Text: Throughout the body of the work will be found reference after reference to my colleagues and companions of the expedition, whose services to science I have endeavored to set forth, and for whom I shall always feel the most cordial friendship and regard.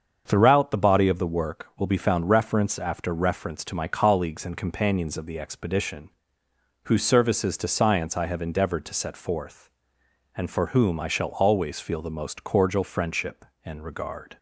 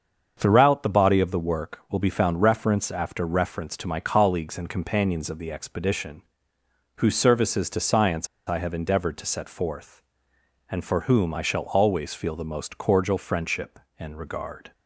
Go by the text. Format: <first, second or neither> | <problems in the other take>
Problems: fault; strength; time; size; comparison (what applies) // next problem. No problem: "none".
first | starts louder than the rest; until 1.3 s; 7 dB; also in the first // pauses between "science" and "I"; slight; at 8.2 s; 0.20 s long